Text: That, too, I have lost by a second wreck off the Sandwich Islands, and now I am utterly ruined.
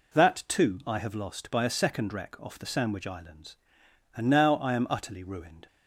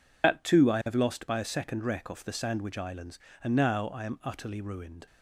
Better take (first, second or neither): first